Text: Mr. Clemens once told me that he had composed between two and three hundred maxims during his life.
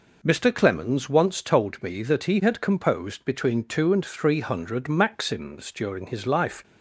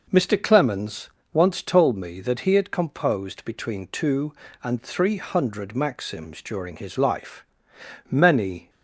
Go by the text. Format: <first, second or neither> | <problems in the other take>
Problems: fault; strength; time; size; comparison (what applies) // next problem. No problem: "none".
first | pauses between "Clemens" and "once"; slight; at 1.1 s; 0.23 s long // goes on to say "Many"; noticeable; from 8.0 s on; 0.62 s long